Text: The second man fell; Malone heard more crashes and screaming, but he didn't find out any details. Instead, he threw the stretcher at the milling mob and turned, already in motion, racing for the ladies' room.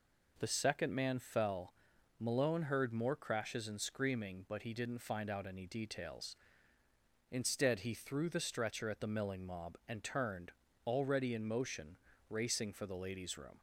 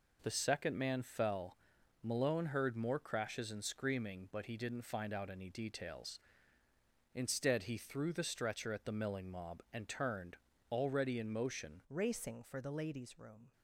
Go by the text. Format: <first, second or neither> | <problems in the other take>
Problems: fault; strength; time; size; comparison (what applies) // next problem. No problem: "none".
first | changes voice at "racing"; from 11.8 s on; 1.7 s long